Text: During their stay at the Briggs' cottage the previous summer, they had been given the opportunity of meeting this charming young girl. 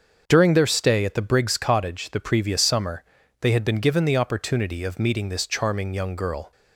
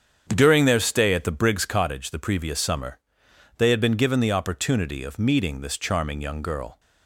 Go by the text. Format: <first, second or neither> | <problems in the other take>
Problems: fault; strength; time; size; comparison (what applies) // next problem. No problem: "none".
neither | starts louder than the rest; the same in both